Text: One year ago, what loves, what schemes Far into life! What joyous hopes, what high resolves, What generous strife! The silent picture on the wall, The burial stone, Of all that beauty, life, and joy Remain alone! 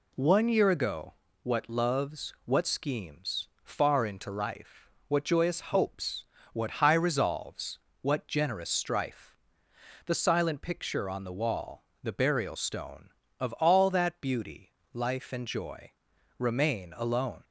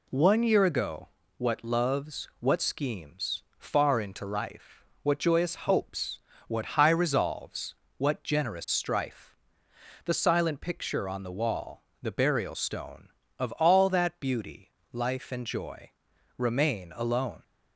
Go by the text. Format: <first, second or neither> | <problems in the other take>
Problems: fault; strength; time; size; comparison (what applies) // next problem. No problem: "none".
neither | pauses between "schemes" and "Far"; slight; the same in both // pauses between "joy" and "Remain"; noticeable; the same in both